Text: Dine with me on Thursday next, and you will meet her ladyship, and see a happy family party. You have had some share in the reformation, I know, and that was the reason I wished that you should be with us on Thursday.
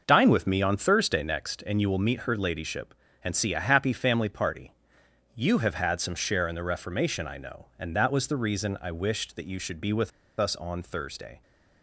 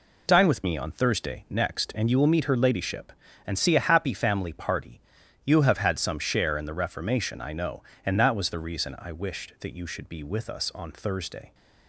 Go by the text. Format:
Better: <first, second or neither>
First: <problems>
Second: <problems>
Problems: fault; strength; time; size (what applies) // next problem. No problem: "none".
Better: second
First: starts louder than the rest; noticeable; until 1.0 s; 6 dB // pauses between "with" and "us"; slight; at 10.1 s; 0.29 s long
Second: none